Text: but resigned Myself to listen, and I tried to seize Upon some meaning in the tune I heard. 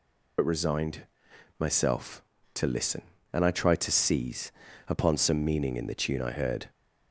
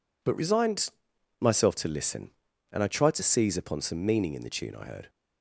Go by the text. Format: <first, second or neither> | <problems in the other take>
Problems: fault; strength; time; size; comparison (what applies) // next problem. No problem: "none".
second | loses the start of "but"; at 0.3 s; 60 ms // pauses between "resigned" and "Myself"; noticeable; at 1.0 s; 0.56 s long; noticeable in the second // pauses between "seize" and "Upon"; slight; at 4.5 s; 0.34 s long